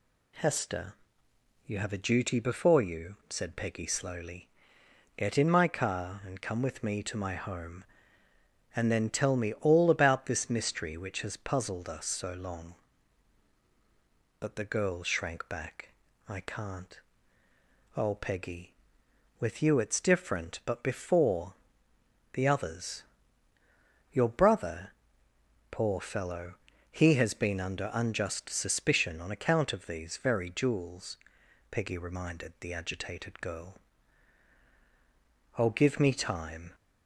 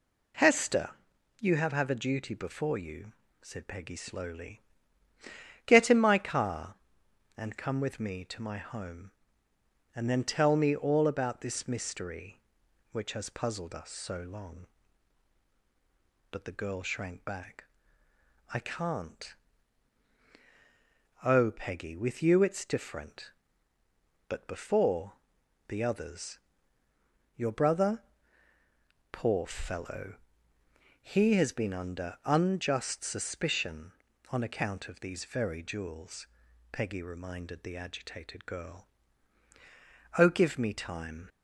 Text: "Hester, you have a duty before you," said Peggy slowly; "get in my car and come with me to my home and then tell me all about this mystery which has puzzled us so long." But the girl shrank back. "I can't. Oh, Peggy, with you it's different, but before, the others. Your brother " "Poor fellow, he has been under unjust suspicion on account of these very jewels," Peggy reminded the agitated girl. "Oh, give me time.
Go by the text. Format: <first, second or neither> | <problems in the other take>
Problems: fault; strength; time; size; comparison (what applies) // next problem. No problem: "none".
first | says "have" twice; at 1.7 s